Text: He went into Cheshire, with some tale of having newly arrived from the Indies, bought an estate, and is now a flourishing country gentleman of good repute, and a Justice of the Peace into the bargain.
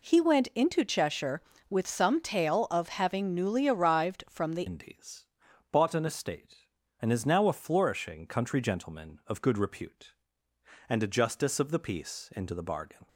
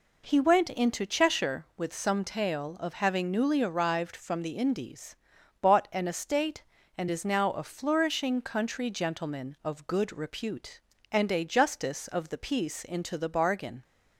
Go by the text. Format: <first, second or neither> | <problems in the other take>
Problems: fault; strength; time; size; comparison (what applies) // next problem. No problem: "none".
second | changes voice at "Indies"; from 4.6 s on; 8.4 s long